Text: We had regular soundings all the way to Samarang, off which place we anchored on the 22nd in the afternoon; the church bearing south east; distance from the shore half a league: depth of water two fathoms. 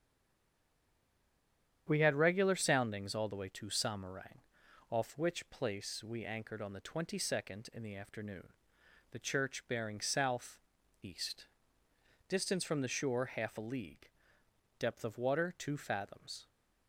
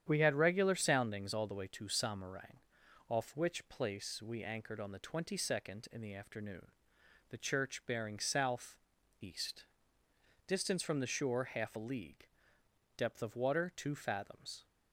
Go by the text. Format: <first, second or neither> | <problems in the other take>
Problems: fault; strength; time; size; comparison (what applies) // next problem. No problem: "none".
second | stays silent before the first word; noticeable; until 1.8 s; 1.8 s long // starts louder than the rest; strong; until 2.8 s; 9 dB; strong in the second // pauses between "south" and "east"; at 10.5 s; 0.44 s long; also in the second